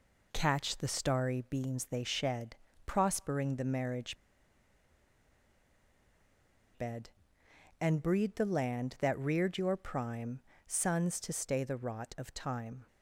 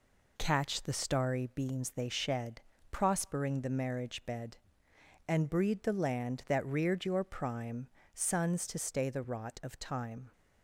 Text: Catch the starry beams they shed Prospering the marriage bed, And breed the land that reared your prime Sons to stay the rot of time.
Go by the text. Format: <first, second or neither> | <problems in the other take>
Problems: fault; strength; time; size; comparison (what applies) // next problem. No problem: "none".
second | pauses between "shed" and "Prospering"; slight; at 2.5 s; 0.32 s long; slight in the second // pauses between "marriage" and "bed"; strong; at 4.1 s; 2.6 s long // pauses between "prime" and "Sons"; slight; at 10.4 s; 0.24 s long; slight in the second